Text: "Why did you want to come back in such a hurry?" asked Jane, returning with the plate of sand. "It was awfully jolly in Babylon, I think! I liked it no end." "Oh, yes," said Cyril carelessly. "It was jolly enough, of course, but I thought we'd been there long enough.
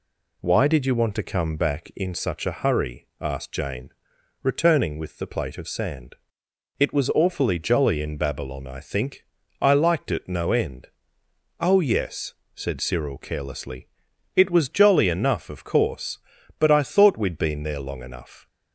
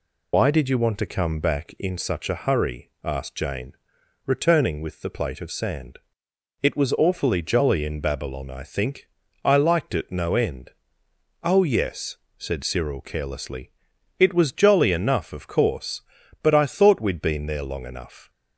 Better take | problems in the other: first | loses the start of "Why"; at 0.3 s; 100 ms

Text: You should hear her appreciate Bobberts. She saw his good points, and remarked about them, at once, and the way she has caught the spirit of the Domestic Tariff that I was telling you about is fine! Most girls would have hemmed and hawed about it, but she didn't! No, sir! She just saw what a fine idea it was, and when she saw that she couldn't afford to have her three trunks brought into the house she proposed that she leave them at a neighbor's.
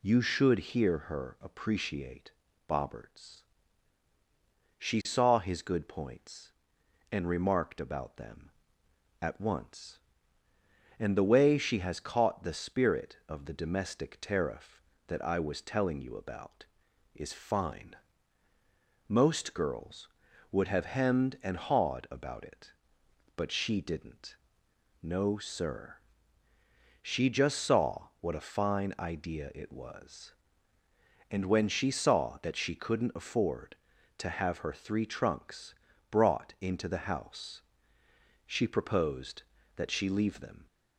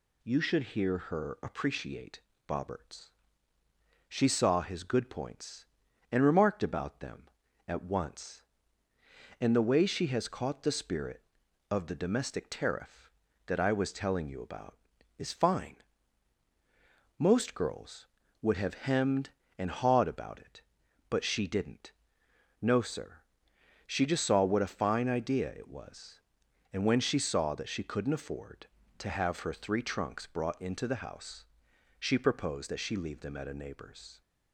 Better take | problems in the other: second | pauses between "appreciate" and "Bobberts"; slight; at 2.3 s; 0.36 s long; slight in the second // pauses between "trunks" and "brought"; slight; at 35.7 s; 0.36 s long // pauses between "house" and "she"; noticeable; at 37.6 s; 0.84 s long; noticeable in the second // stops before "at a neighbor's"; at 40.6 s

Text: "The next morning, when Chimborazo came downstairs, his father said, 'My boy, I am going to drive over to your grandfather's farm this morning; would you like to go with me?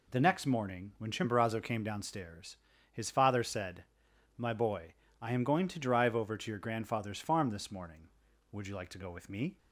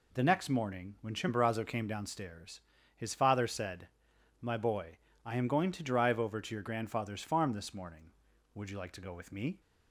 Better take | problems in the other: neither | none

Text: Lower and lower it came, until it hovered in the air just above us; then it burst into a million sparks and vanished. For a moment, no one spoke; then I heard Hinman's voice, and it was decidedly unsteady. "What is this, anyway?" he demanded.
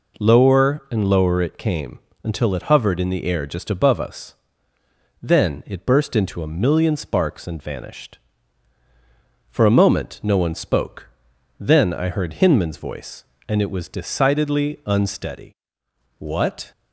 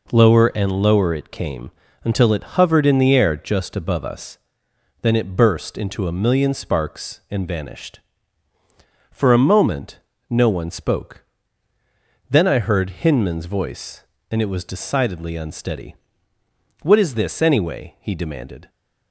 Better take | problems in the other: second | stops before "is this anyway he demanded"; at 16.7 s

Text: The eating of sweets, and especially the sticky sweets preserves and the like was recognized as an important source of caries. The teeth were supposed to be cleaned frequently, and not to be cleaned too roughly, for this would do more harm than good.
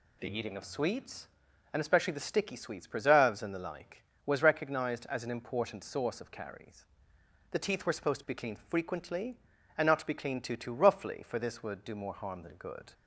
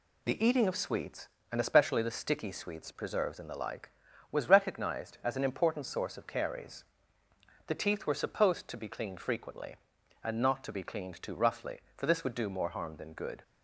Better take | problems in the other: second | says "too" twice; at 10.5 s

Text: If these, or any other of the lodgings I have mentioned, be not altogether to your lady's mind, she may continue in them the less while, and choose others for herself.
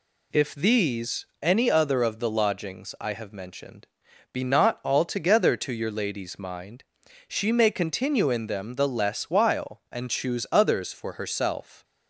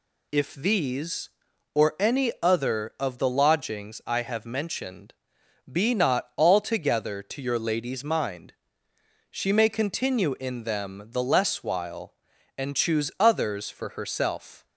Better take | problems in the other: second | skips "or"; at 1.3 s

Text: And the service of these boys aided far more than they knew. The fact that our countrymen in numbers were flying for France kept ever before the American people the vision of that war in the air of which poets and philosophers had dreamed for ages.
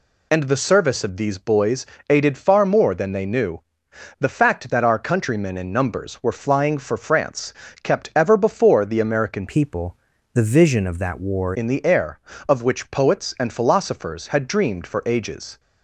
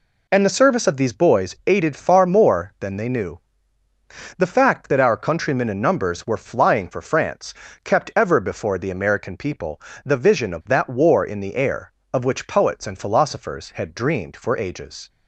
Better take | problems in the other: second | pauses between "boys" and "aided"; slight; at 1.8 s; 0.24 s long // pauses between "France" and "kept"; slight; at 7.5 s; 0.30 s long; slight in the second // changes voice from "people" to "war"; from 9.4 to 11.5 s; 2.1 s long // pauses between "people" and "the"; at 9.9 s; 0.38 s long; slight in the second

